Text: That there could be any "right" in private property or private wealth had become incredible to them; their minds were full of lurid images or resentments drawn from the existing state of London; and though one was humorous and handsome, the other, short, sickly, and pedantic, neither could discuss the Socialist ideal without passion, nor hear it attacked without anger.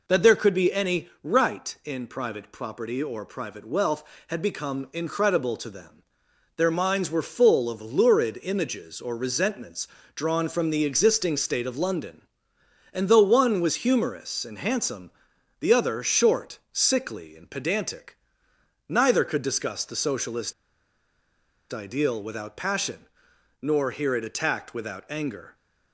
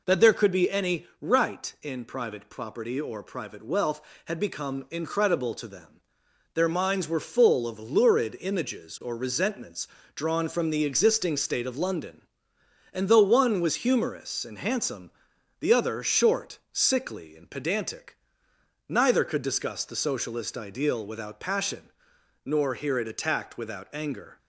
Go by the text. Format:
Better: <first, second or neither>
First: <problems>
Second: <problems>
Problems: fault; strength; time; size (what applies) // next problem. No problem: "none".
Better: second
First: pauses between "resentments" and "drawn"; slight; at 9.8 s; 0.26 s long // pauses between "Socialist" and "ideal"; at 20.5 s; 1.1 s long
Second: pauses between "resentments" and "drawn"; slight; at 9.8 s; 0.26 s long